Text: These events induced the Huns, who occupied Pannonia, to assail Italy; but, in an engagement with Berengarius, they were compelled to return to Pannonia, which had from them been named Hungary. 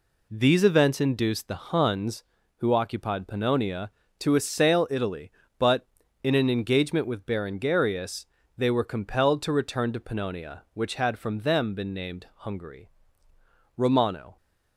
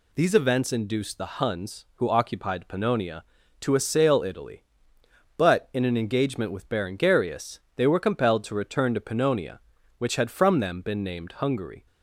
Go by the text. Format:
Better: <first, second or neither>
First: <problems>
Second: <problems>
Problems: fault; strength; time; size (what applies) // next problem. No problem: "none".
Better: second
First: goes on to say "Romano"; from 13.7 s on; 0.60 s long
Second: none